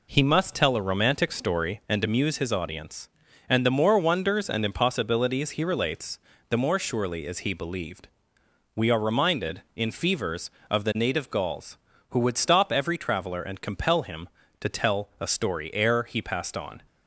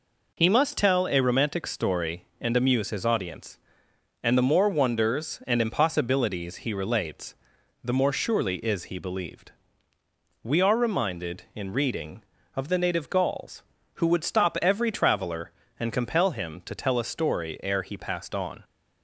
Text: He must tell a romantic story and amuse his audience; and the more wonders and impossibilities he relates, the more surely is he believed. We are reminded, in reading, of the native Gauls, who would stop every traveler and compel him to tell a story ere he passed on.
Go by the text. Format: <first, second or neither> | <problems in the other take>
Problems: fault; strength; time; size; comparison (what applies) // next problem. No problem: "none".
second | says "fevers" for "reading"; at 9.9 s